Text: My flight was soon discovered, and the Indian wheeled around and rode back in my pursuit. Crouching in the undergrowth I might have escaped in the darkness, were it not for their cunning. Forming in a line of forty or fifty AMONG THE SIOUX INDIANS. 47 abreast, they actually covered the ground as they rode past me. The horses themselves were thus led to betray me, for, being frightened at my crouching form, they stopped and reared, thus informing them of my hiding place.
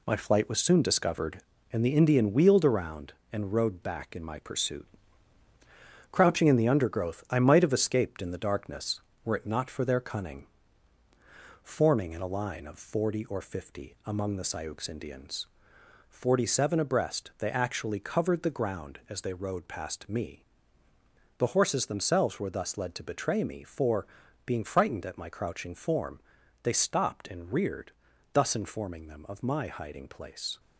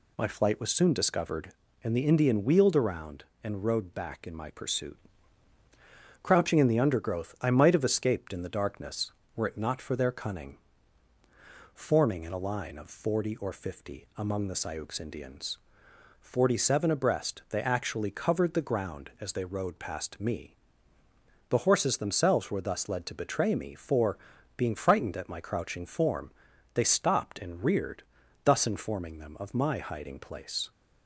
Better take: second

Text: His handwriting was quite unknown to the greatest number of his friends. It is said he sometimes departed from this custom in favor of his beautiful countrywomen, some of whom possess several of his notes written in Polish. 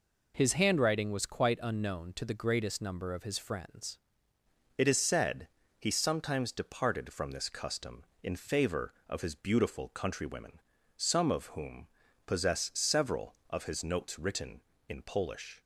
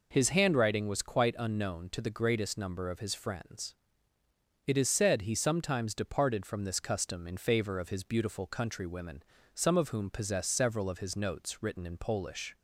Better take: second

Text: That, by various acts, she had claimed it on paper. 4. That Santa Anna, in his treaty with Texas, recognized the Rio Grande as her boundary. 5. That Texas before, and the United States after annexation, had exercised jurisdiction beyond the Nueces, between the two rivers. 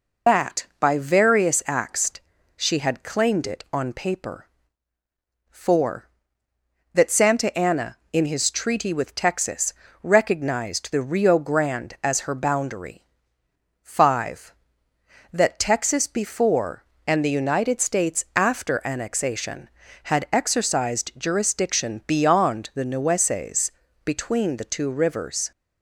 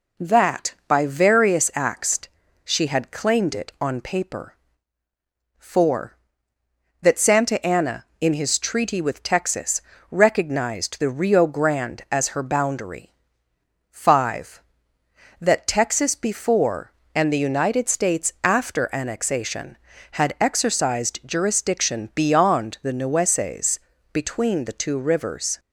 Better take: second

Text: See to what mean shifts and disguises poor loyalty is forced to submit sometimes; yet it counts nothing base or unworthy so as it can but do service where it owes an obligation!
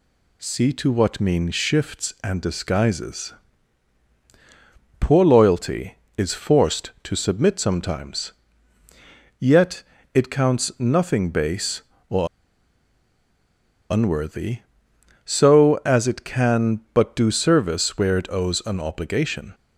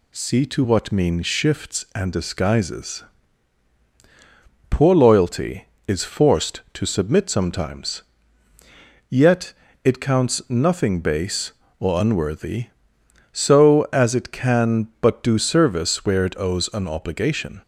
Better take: second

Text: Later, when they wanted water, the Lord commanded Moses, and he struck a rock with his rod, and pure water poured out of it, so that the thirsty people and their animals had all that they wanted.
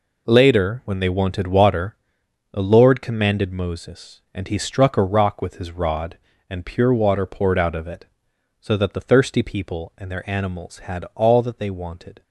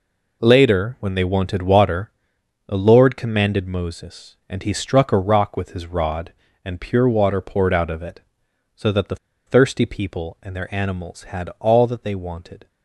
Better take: first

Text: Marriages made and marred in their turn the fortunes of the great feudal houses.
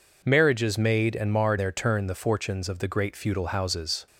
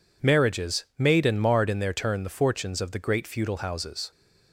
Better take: second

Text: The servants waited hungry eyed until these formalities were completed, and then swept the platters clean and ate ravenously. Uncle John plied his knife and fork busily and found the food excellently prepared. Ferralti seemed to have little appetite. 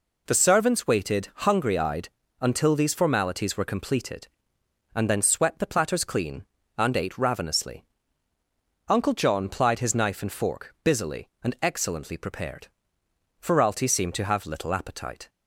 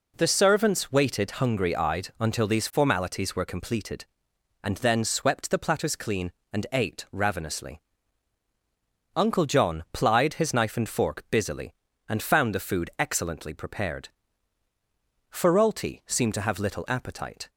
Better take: second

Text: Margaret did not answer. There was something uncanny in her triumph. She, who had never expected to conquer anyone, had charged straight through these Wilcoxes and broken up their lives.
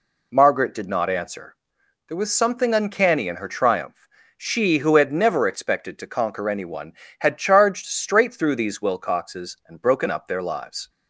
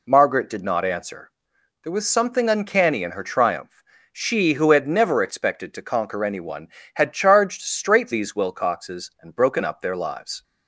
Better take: first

